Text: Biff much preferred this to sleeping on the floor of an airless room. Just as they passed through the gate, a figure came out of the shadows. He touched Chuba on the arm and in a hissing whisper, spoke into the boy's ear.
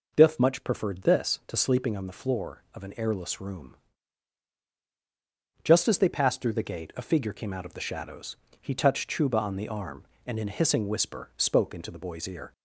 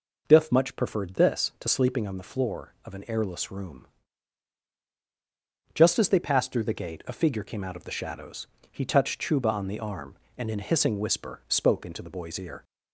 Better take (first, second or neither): neither